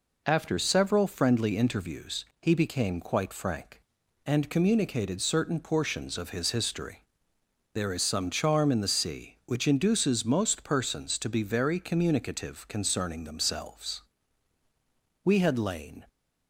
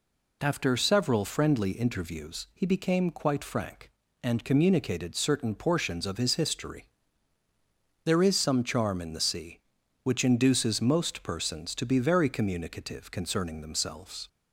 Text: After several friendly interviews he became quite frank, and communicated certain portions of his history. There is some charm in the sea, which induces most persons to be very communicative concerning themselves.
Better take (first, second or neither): second